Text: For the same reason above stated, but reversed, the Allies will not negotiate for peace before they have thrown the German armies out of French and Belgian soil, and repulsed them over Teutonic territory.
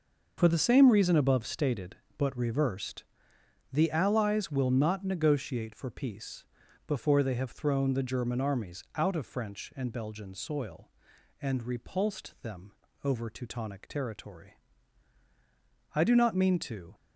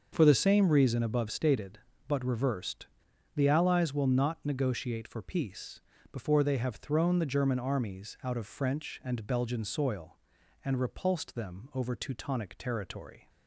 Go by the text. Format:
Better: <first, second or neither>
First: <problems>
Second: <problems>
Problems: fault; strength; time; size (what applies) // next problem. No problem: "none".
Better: second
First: starts louder than the rest; noticeable; until 1.3 s; 6 dB // pauses between "peace" and "before"; at 6.4 s; 0.42 s long // pauses between "them" and "over"; slight; at 12.6 s; 0.34 s long // goes on to say "I do not mean to"; noticeable; from 15.9 s on; 0.98 s long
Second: starts louder than the rest; until 1.1 s; 6 dB // pauses between "peace" and "before"; slight; at 5.8 s; 0.28 s long